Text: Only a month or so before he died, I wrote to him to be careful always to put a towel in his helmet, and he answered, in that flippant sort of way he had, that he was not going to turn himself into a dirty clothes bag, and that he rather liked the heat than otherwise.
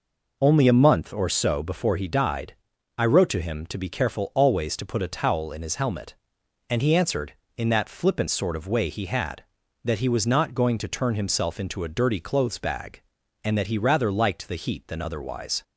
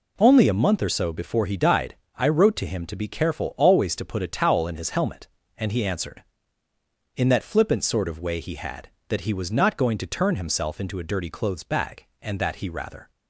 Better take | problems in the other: first | stops before "liked the heat than otherwise"; at 13.1 s

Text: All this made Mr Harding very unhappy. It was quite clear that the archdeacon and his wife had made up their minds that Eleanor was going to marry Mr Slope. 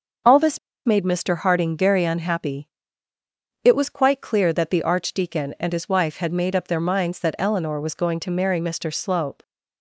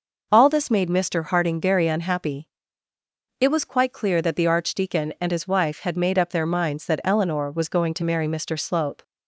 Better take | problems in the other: second | starts louder than the rest; until 1.5 s; 6.5 dB // pauses between "this" and "made"; slight; at 0.5 s; 0.27 s long

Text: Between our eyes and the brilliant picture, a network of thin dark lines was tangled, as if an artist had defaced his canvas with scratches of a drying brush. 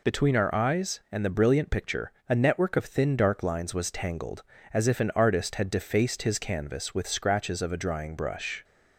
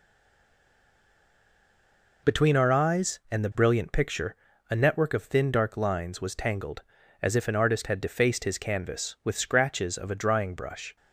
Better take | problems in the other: first | stays silent before the first word; until 2.2 s; 2.2 s long

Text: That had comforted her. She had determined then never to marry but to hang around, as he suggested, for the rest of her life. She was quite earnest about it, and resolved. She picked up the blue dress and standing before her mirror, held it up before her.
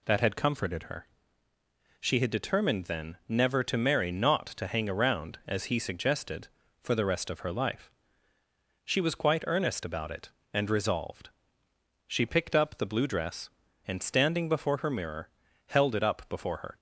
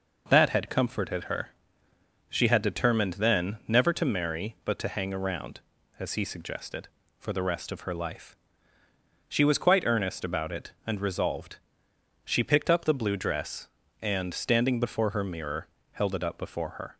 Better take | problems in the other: second | says "not" for "but"; at 4.1 s

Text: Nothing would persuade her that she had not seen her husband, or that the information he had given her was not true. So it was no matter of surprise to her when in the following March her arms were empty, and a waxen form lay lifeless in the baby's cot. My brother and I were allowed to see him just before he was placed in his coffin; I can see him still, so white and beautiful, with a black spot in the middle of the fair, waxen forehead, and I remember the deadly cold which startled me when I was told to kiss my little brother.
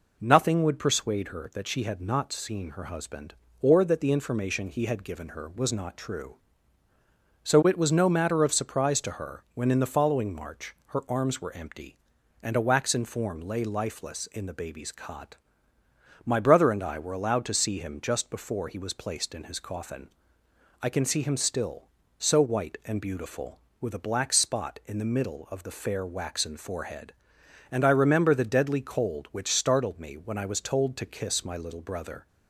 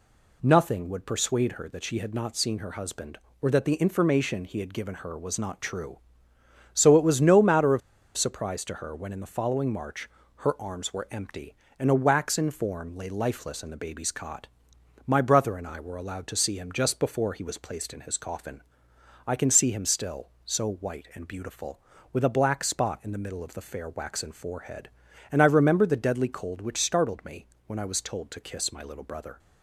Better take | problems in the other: first | pauses between "of" and "surprise"; at 7.8 s; 0.36 s long // pauses between "March" and "her"; slight; at 10.0 s; 0.28 s long // pauses between "me" and "when"; slight; at 27.4 s; 0.22 s long

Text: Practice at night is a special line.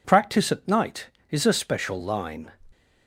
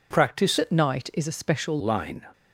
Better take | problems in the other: first | changes voice from "at" to "special"; from 0.5 to 1.7 s; 1.2 s long

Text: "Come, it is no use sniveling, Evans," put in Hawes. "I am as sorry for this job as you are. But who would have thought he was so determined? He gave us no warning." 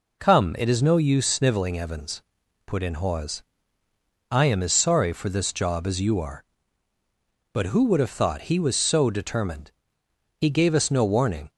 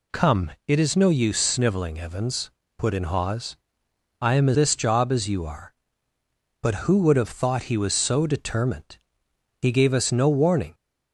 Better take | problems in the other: first | skips "sorry for"; at 4.5 s

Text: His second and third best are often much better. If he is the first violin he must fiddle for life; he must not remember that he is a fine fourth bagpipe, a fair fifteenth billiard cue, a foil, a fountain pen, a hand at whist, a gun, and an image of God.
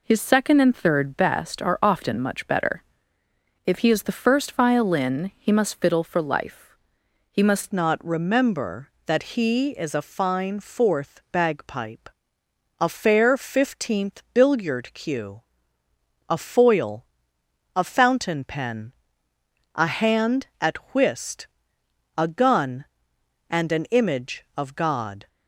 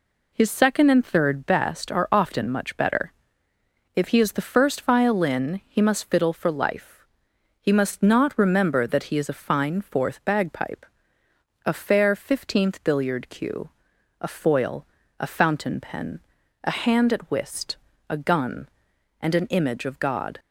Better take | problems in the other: second | changes voice at "not"; from 7.7 s on; 17.5 s long // pauses between "at" and "whist"; slight; at 20.7 s; 0.18 s long

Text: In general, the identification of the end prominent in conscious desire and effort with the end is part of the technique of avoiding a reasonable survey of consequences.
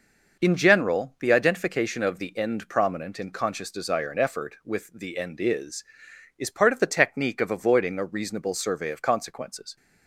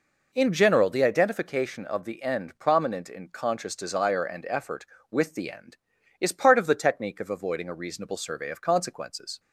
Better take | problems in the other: second | says "is" twice; at 6.3 s

